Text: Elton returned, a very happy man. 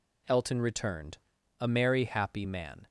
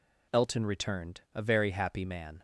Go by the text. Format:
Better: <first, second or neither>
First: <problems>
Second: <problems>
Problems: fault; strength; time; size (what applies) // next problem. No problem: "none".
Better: second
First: says "merry" for "very"; at 1.6 s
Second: none